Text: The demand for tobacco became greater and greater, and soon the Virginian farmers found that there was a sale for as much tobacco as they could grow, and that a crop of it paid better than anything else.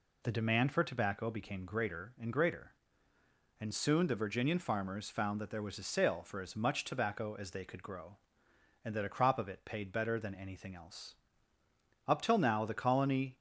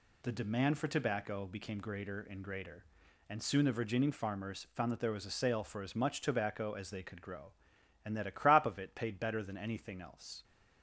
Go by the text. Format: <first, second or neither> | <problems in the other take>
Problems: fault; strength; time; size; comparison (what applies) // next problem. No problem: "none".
second | goes on to say "Up till now the colony"; from 12.0 s on; 1.3 s long